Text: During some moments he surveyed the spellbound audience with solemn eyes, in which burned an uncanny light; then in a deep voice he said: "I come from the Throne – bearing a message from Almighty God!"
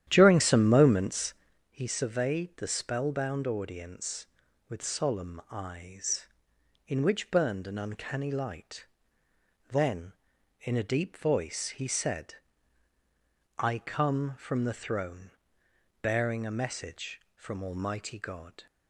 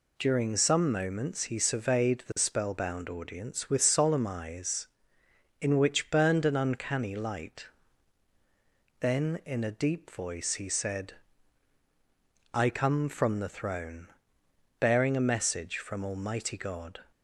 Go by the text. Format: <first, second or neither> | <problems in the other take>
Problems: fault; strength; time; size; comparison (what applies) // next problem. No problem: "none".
second | starts louder than the rest; strong; until 1.6 s; 11 dB // pauses between "moments" and "he"; at 1.3 s; 0.38 s long